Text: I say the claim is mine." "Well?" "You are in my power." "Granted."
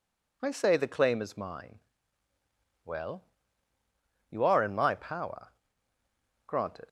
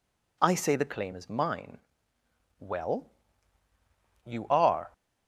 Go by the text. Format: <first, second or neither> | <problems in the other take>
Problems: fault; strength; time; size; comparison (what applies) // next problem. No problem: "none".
first | stops before "in my power Granted"; at 4.9 s